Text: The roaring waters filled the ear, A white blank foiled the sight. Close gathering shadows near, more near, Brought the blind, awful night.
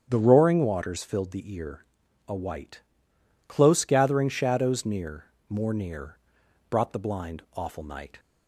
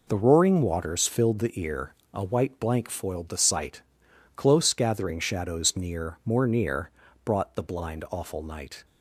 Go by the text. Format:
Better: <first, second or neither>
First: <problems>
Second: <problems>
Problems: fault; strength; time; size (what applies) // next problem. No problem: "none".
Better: second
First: starts louder than the rest; strong; until 1.1 s; 8 dB // skips "blank foiled the sight"; at 3.1 s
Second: none